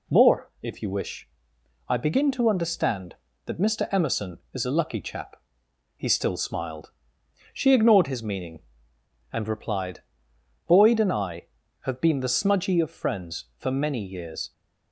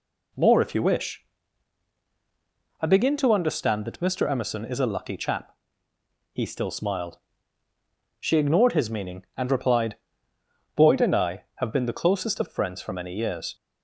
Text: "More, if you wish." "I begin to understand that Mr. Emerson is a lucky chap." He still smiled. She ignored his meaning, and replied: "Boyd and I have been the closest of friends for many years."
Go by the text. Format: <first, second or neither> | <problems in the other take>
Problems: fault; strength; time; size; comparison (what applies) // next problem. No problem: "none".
second | says "smudgy" for "closest"; at 12.2 s